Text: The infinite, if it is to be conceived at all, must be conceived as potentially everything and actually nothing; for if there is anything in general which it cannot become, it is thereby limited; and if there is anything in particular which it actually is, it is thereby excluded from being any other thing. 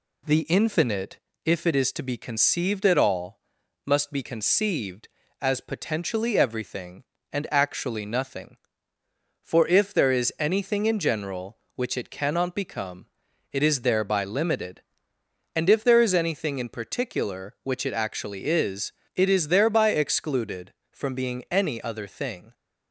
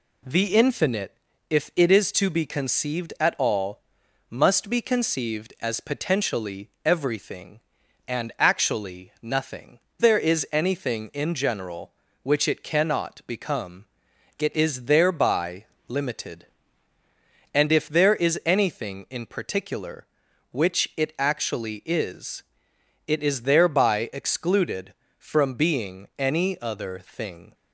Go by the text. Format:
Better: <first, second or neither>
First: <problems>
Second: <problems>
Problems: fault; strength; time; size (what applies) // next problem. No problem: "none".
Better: first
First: none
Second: skips "for if"; at 9.8 s // pauses between "thereby" and "limited"; slight; at 15.6 s; 0.24 s long